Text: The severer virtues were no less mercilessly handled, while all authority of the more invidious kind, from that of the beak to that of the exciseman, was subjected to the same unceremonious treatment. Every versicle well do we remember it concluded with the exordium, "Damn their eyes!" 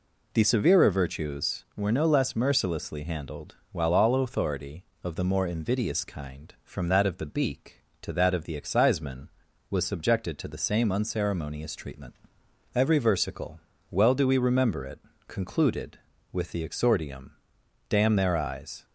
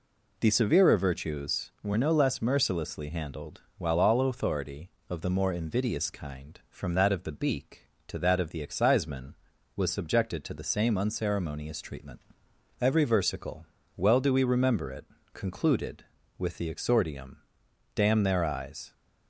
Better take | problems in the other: neither | pauses between "versicle" and "well"; slight; the same in both // pauses between "it" and "concluded"; slight; the same in both

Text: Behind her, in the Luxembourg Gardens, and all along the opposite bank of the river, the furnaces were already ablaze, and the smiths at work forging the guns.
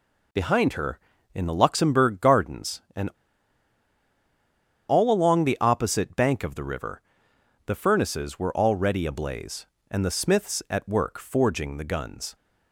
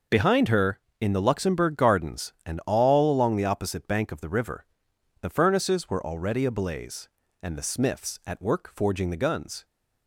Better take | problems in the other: second | pauses between "and" and "all"; strong; at 3.0 s; 1.8 s long

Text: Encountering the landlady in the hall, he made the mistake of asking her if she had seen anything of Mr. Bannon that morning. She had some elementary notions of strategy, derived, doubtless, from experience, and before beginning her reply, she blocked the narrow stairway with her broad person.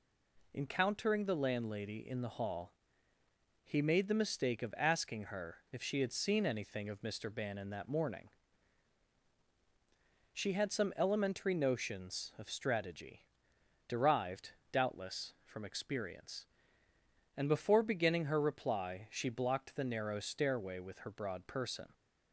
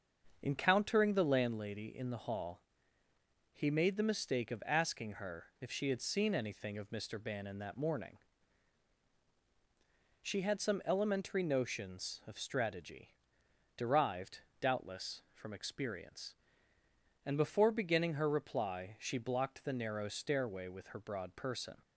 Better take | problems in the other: first | starts louder than the rest; until 1.5 s; 6.5 dB

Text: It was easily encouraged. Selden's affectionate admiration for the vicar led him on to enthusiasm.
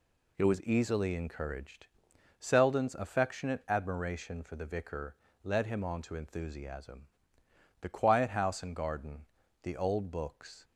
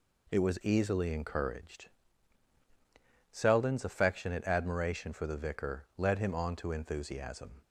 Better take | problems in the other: second | pauses between "vicar" and "led"; slight; at 5.1 s; 0.28 s long // goes on to say "The quiet house and garden the old books"; strong; from 7.8 s on; 2.8 s long

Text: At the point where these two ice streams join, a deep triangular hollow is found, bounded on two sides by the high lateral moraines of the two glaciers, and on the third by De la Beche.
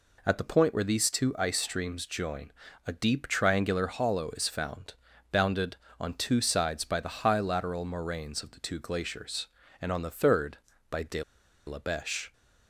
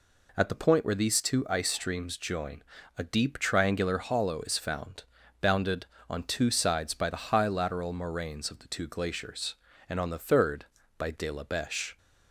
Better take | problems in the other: second | pauses between "De" and "la"; at 11.2 s; 0.45 s long

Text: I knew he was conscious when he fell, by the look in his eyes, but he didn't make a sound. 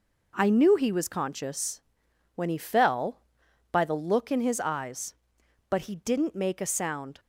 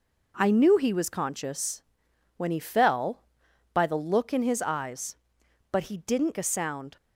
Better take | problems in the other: first | pauses between "conscious" and "when"; noticeable; at 1.8 s; 0.54 s long; noticeable in the first // skips "make"; at 6.3 s

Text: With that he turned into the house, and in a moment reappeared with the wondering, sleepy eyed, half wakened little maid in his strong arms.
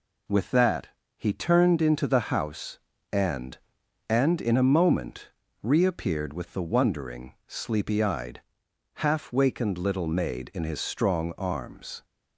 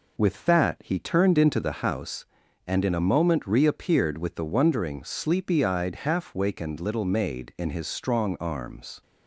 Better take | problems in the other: second | pauses between "that" and "he"; slight; at 0.8 s; 0.28 s long // says "and" twice; at 4.0 s // pauses between "moment" and "reappeared"; slight; at 5.3 s; 0.32 s long

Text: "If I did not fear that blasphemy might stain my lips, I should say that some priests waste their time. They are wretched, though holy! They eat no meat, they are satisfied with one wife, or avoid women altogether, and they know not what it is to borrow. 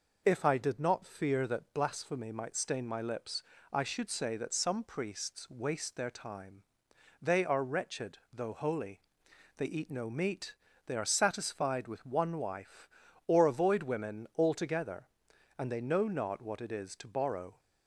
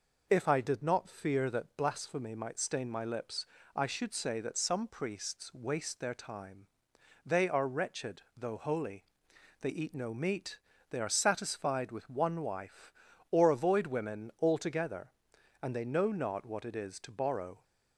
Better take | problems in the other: neither | none

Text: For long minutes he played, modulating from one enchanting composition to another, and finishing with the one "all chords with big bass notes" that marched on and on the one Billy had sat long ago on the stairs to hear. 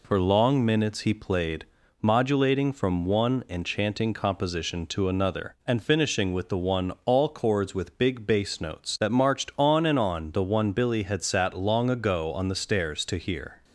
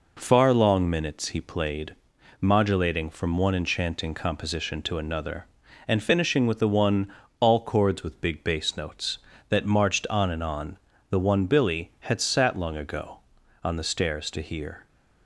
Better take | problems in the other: first | says "Far" for "For"; at 0.1 s // pauses between "one" and "all"; slight; at 7.1 s; 0.26 s long // pauses between "on" and "the"; slight; at 10.7 s; 0.32 s long

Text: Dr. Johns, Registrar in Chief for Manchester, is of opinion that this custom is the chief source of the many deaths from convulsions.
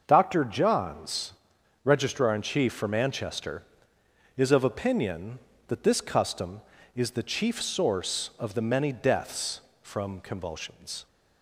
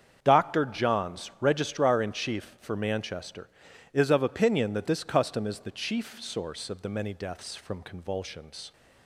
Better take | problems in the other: neither | starts louder than the rest; the same in both

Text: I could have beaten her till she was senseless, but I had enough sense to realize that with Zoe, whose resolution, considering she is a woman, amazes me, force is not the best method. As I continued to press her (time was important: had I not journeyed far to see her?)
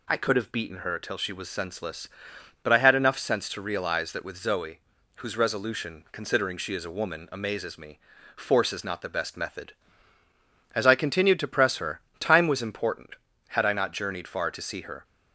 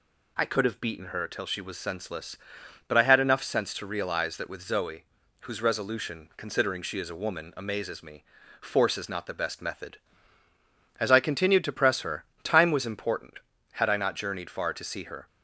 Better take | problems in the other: neither | none

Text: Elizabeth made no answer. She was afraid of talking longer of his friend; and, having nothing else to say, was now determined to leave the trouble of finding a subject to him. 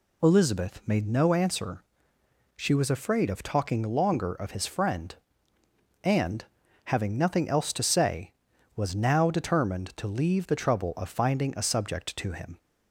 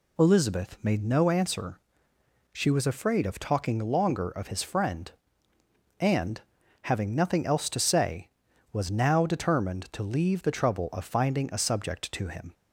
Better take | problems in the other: neither | none

